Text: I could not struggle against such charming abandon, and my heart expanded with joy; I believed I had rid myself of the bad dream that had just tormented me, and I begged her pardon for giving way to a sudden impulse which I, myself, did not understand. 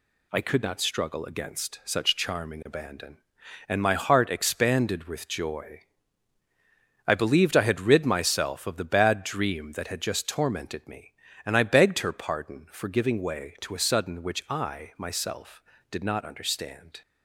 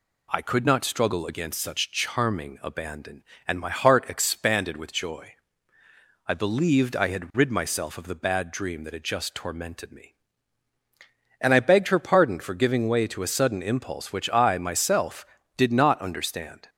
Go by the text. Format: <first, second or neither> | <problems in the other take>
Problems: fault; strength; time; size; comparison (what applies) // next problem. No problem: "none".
second | skips "impulse"; at 14.2 s